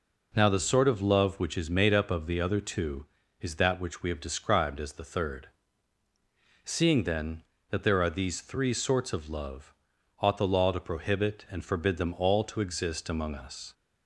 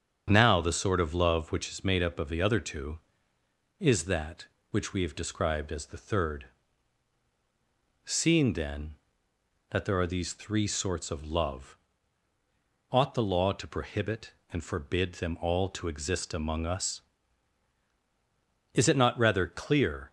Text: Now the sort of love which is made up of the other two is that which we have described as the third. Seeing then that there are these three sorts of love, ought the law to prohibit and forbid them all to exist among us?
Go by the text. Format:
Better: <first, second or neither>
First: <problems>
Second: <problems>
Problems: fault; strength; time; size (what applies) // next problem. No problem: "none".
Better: first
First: none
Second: starts louder than the rest; strong; until 1.2 s; 8 dB // goes on to say "Is it not rather clear"; from 18.7 s on; 1.3 s long